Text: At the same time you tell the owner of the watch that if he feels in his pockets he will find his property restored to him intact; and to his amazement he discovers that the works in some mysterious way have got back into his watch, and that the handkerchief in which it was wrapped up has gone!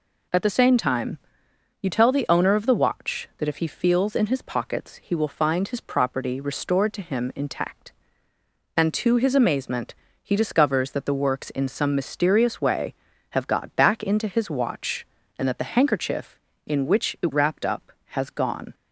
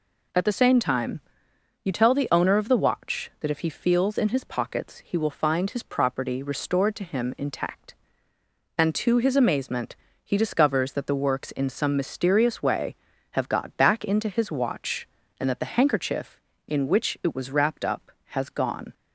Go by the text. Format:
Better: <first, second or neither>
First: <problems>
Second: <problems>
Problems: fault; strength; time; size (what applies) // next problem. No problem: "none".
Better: second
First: pauses between "time" and "you"; noticeable; at 1.1 s; 0.62 s long // pauses between "amazement" and "he"; slight; at 9.9 s; 0.28 s long // skips "was"; at 17.3 s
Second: pauses between "time" and "you"; noticeable; at 1.2 s; 0.62 s long // pauses between "amazement" and "he"; slight; at 9.9 s; 0.28 s long